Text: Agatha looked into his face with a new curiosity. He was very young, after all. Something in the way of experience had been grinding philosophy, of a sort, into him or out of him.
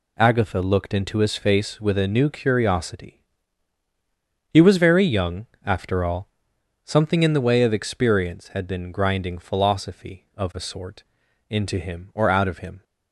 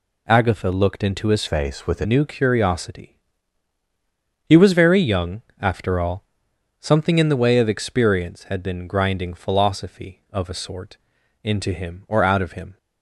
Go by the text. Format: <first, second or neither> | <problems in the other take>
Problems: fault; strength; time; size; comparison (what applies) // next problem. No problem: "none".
first | changes voice from "face" to "a"; from 1.4 to 2.0 s; 0.6 s long